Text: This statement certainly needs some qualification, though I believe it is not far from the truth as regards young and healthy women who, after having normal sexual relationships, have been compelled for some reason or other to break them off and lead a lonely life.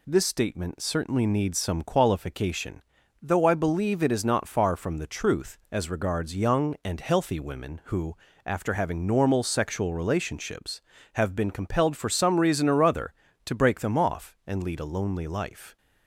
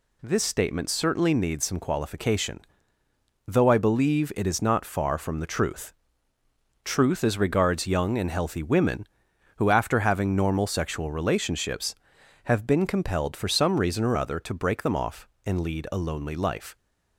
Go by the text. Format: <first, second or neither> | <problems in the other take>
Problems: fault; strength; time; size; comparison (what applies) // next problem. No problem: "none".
first | says "truth" twice; at 6.8 s